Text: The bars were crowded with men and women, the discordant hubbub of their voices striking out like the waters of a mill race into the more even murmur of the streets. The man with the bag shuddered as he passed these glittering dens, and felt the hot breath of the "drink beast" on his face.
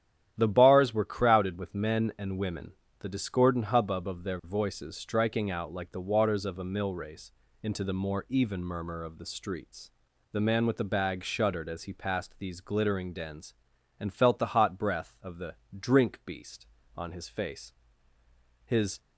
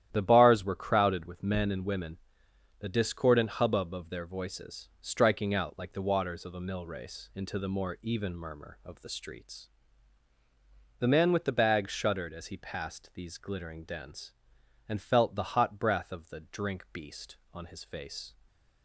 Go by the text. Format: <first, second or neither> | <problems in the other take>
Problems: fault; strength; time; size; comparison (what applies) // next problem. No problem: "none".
second | starts louder than the rest; strong; until 1.3 s; 10.5 dB; strong in the second // pauses between "race" and "into"; slight; at 7.3 s; 0.32 s long // pauses between "the" and "drink"; slight; at 15.5 s; 0.22 s long // goes on to say "His"; slight; from 18.6 s on; 0.34 s long